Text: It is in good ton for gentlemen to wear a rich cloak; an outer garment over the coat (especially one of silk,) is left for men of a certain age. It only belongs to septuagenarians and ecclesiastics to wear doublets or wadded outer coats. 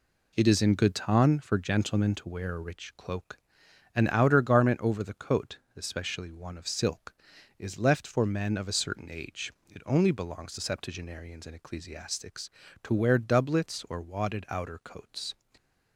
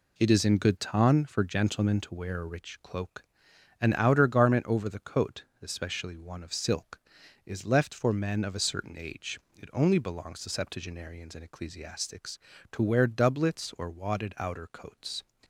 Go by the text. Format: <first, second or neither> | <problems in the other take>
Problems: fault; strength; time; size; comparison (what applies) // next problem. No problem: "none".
neither | none